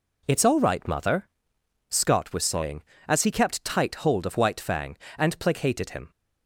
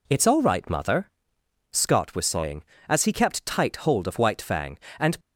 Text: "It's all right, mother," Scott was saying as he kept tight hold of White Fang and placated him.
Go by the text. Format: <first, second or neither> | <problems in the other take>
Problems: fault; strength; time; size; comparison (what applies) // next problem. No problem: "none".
first | stops before "placated him"; at 5.1 s